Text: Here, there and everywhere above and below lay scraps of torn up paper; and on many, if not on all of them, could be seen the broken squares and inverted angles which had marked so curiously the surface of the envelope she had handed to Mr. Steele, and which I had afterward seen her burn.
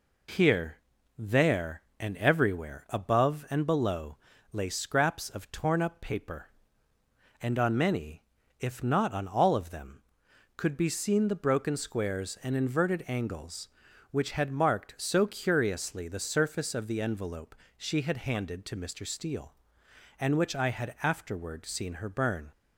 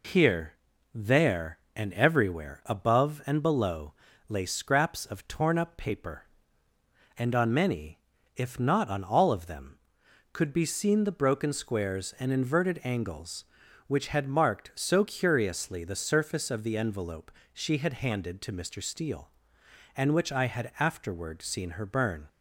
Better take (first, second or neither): neither